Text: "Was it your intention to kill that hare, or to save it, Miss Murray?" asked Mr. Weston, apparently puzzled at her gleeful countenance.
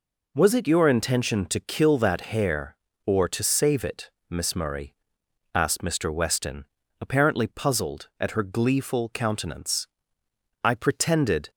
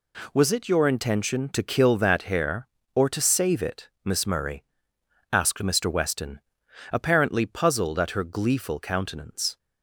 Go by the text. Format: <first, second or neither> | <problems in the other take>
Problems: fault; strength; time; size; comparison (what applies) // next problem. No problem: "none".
second | goes on to say "I pretended"; noticeable; from 10.6 s on; 0.86 s long